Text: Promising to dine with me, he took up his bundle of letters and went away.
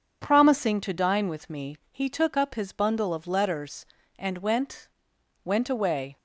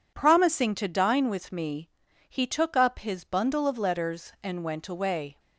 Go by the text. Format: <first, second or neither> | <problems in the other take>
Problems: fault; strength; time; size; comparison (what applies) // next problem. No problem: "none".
second | says "went" twice; at 5.4 s